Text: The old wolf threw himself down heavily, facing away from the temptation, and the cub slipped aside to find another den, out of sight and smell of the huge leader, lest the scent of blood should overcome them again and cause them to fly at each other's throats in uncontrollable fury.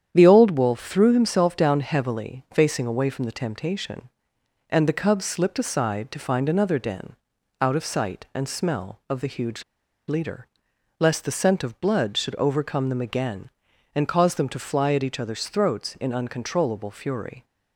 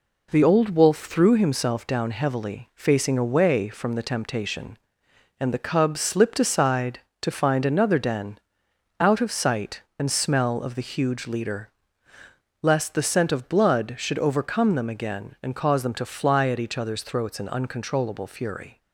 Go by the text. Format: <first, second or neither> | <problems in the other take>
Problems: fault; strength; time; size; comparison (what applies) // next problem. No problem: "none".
second | starts louder than the rest; strong; until 1.1 s; 9 dB // pauses between "huge" and "leader"; at 9.6 s; 0.45 s long